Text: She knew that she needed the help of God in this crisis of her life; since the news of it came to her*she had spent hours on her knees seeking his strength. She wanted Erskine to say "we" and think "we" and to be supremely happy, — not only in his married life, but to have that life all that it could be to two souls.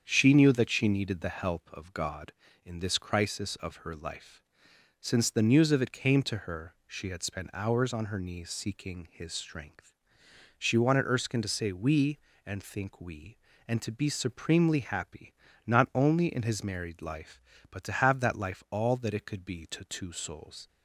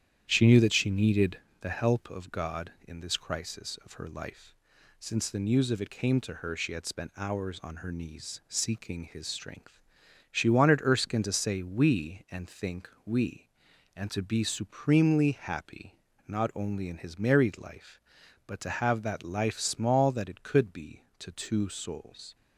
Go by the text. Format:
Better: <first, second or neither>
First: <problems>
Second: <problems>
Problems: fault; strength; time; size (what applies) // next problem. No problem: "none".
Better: first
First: starts louder than the rest; strong; until 1.0 s; 7.5 dB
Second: starts louder than the rest; strong; until 1.2 s; 10 dB // pauses between "needed" and "the"; slight; at 1.3 s; 0.22 s long // pauses between "think" and "we"; slight; at 12.9 s; 0.16 s long // says "small" for "all"; at 19.5 s